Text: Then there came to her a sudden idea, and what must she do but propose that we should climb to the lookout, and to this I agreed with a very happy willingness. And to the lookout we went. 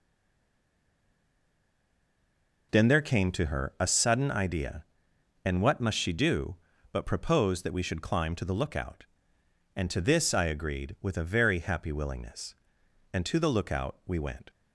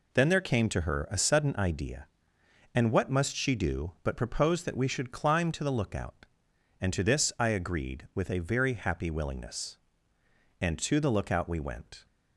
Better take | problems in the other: second | stays silent before the first word; strong; until 2.7 s; 2.7 s long

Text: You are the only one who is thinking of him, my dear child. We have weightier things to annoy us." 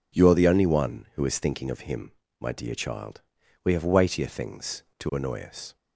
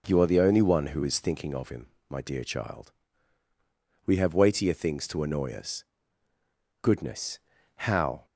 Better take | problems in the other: first | goes on to say "Goodness how"; from 6.8 s on; 1.4 s long

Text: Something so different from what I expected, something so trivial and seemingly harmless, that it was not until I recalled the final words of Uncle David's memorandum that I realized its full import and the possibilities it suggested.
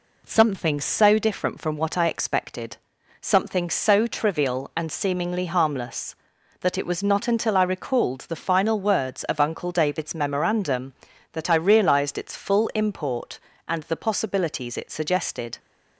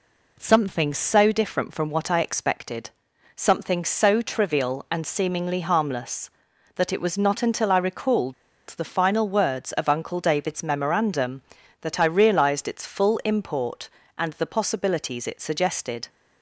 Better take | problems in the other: first | pauses between "recalled" and "the"; at 8.3 s; 0.36 s long

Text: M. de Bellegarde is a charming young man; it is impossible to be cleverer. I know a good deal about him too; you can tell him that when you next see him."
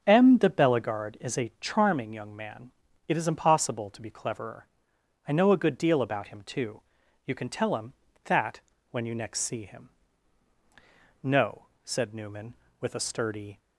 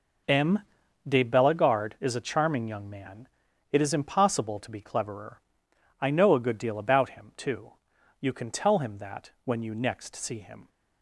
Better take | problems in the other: second | starts louder than the rest; until 1.0 s; 7 dB // pauses between "that" and "when"; slight; at 8.6 s; 0.28 s long // goes on to say "No said Newman with a sturdy"; strong; from 11.2 s on; 2.3 s long

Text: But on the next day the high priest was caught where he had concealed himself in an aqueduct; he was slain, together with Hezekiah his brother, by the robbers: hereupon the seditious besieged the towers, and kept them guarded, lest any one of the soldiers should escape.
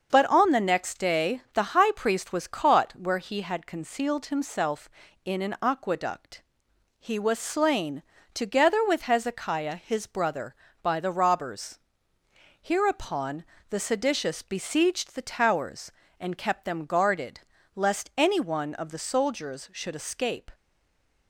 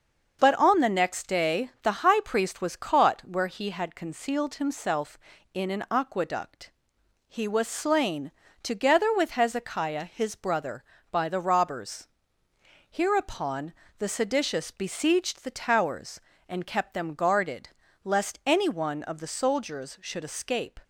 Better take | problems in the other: second | starts louder than the rest; until 1.1 s; 6.5 dB; also in the second // pauses between "hereupon" and "the"; slight; at 13.4 s; 0.24 s long; slight in the second // stays silent after the last word; slight; from 20.5 s on; 0.7 s long

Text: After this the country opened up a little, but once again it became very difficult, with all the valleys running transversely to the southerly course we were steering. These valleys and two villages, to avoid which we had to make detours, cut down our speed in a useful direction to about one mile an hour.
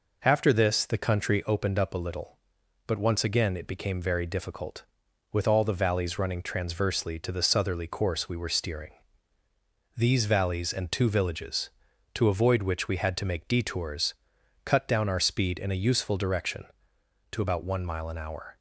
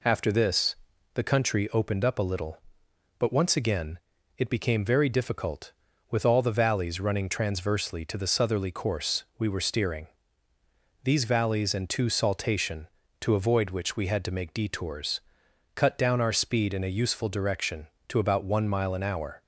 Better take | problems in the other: first | pauses between "this" and "the"; at 0.7 s; 0.38 s long // pauses between "again" and "it"; at 3.9 s; 0.40 s long // says "saltation" for "villages"; at 12.0 s

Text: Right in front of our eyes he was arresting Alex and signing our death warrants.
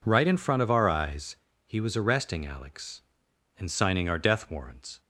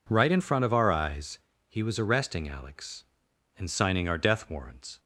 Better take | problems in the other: neither | pauses between "eyes" and "he"; slight; the same in both

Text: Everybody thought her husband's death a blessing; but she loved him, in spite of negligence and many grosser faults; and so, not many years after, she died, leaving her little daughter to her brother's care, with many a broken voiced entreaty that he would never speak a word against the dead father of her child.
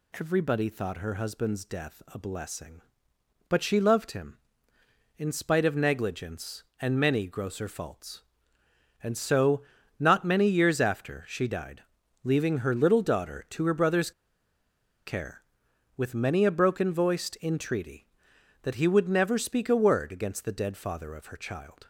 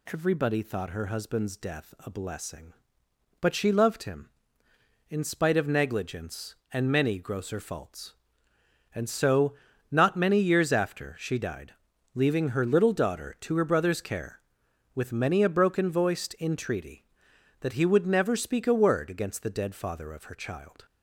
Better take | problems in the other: second | pauses between "brother's" and "care"; noticeable; at 14.1 s; 0.95 s long

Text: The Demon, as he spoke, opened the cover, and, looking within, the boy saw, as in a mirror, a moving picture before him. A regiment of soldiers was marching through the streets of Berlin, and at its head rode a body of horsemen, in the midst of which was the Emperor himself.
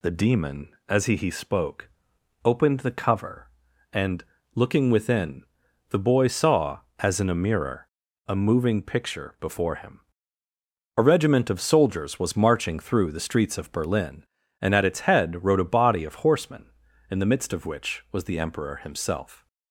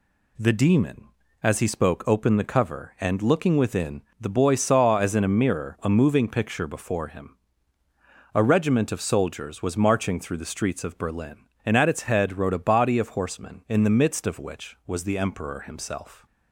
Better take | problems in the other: second | says "he" twice; at 1.1 s

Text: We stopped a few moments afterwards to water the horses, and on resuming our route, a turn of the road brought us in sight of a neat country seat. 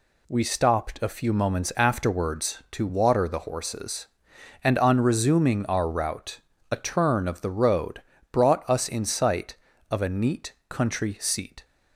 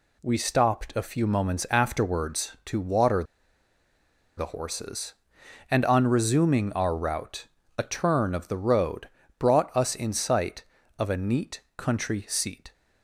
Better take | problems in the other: first | pauses between "water" and "the"; at 3.2 s; 1.1 s long // pauses between "road" and "brought"; slight; at 9.0 s; 0.30 s long; slight in the first // pauses between "neat" and "country"; slight; at 11.6 s; 0.16 s long; slight in the first

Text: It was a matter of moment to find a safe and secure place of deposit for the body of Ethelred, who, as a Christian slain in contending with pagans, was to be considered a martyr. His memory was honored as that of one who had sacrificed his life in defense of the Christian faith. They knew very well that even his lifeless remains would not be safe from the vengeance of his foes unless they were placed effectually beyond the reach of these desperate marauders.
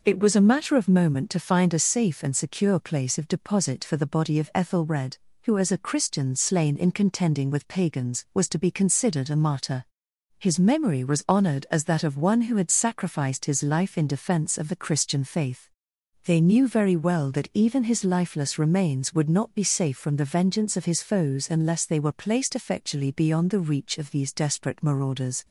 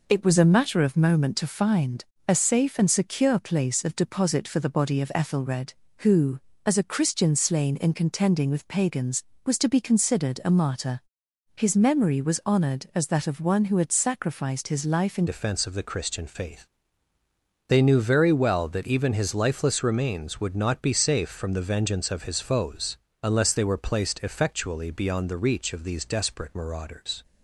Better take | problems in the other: first | pauses between "find" and "a"; slight; at 2.0 s; 0.24 s long // changes voice at "defense"; from 15.2 s on; 12.0 s long // pauses between "foes" and "unless"; slight; at 22.9 s; 0.26 s long

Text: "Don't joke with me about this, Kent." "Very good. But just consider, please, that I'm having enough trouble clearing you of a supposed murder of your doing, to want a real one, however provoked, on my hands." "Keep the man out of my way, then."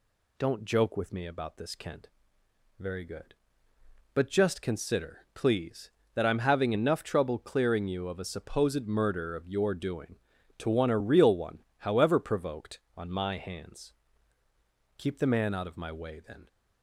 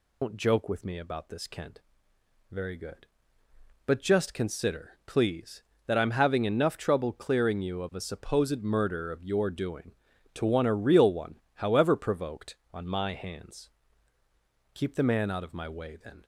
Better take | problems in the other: first | loses the start of "Don't"; at 0.2 s; 115 ms

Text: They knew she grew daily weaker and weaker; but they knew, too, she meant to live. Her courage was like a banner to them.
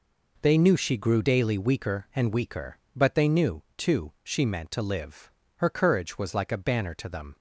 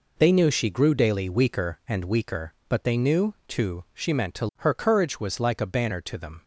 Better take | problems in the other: first | skips "live"; at 4.5 s

